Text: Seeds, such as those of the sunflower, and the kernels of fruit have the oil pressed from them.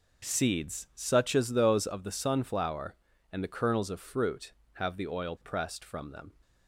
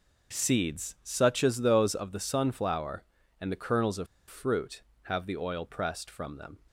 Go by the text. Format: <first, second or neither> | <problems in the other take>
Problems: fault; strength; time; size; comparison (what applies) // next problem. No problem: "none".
first | pauses between "of" and "fruit"; slight; at 4.0 s; 0.22 s long